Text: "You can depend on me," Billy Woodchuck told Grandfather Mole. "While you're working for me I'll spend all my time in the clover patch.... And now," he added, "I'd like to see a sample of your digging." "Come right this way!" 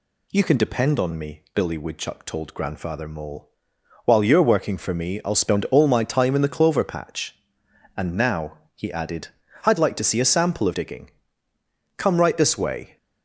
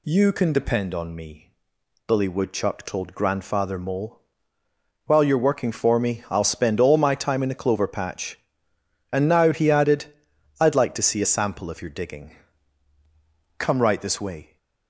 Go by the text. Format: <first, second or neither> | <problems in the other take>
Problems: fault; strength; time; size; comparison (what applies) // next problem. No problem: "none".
second | skips "your"; at 10.7 s